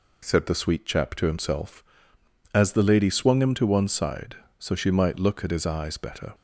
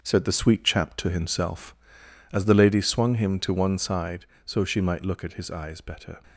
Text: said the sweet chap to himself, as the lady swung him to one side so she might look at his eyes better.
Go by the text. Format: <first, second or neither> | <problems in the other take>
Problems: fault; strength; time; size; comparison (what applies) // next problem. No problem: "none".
first | gets quieter; strong; throughout; 7.5 dB